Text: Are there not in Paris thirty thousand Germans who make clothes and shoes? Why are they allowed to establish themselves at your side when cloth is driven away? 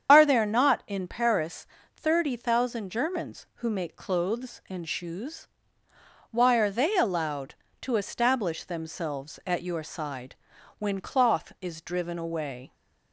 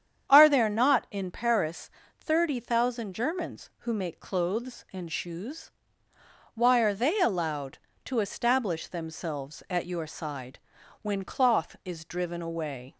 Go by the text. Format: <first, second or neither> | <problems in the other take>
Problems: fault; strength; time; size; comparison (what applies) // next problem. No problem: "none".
second | loses the start of "Are"; at 0.0 s; 40 ms // starts louder than the rest; strong; until 1.1 s; 8 dB; strong in the second // pauses between "Paris" and "thirty"; slight; at 1.6 s; 0.28 s long; slight in the second // pauses between "side" and "when"; at 10.3 s; 0.44 s long; also in the second